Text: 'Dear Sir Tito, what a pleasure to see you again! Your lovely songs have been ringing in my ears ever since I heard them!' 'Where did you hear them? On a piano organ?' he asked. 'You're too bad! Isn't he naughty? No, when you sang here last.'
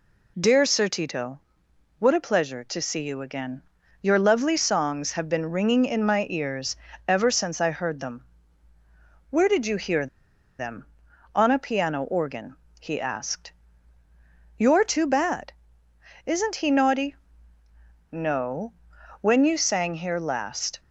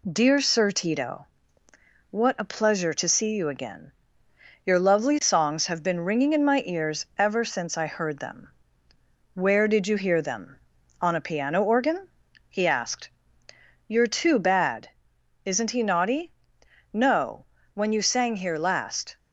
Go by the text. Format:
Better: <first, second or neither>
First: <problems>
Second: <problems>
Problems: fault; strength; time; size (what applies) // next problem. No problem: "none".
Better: second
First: pauses between "ears" and "ever"; slight; at 6.7 s; 0.32 s long // pauses between "hear" and "them"; noticeable; at 10.0 s; 0.53 s long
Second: none